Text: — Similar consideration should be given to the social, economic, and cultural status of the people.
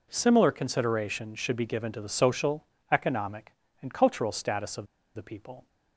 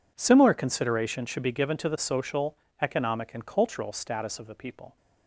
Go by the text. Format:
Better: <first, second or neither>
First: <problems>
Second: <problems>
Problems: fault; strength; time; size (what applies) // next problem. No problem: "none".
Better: second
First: pauses between "of" and "the"; slight; at 4.8 s; 0.29 s long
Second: none